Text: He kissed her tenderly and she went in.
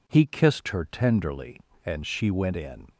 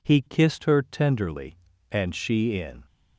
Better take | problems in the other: first | skips "went"; at 2.5 s

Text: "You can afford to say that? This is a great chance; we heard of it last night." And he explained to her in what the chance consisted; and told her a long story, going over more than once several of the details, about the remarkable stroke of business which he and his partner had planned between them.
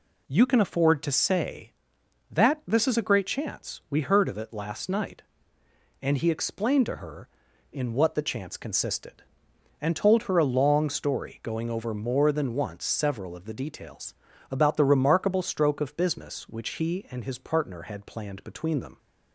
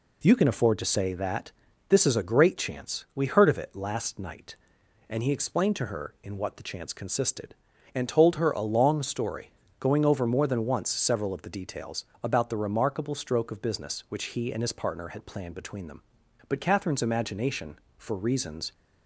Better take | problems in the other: first | goes on to say "But Catherine's imagination for reasons"; strong; from 16.4 s on; 2.2 s long

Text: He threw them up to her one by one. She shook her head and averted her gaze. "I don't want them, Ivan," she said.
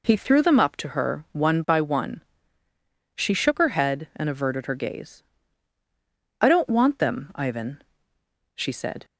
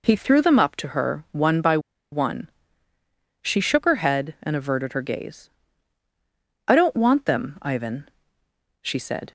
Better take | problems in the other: first | pauses between "by" and "one"; slight; at 1.7 s; 0.33 s long

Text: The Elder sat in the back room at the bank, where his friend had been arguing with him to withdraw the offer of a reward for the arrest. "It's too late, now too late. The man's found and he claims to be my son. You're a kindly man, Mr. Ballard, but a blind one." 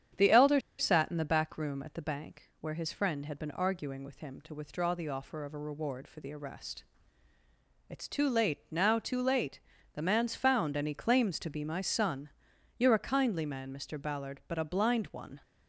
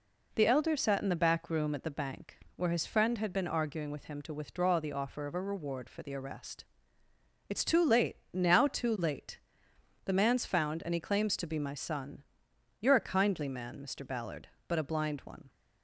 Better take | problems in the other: second | starts louder than the rest; strong; until 1.3 s; 9 dB // pauses between "Elder" and "sat"; slight; at 0.5 s; 0.19 s long

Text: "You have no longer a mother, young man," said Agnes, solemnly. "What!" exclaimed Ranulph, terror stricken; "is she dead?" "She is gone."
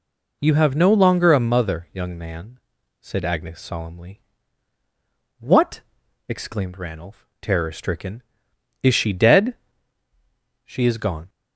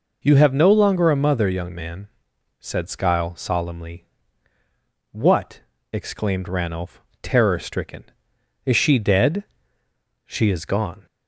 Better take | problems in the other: first | says "Skyle" for "Agnes"; at 2.8 s

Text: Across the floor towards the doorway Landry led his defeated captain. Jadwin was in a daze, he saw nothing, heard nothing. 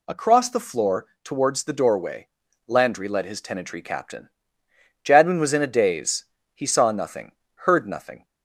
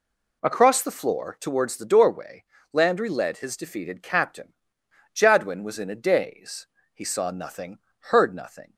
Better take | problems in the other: second | pauses between "floor" and "towards"; slight; at 1.0 s; 0.18 s long // pauses between "doorway" and "Landry"; at 2.2 s; 0.40 s long; slight in the second // says "tenantry" for "defeated"; at 3.4 s

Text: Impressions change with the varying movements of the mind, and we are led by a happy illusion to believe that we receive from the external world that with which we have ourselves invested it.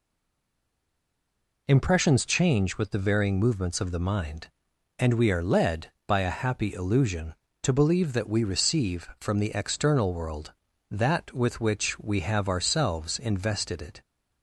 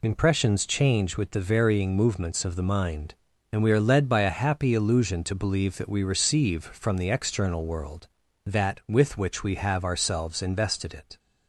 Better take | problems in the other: second | stays silent before the first word; noticeable; until 1.6 s; 1.6 s long

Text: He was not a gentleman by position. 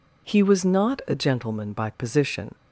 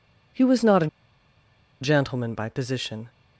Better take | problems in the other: first | pauses between "a" and "gentleman"; noticeable; at 0.8 s; 0.94 s long

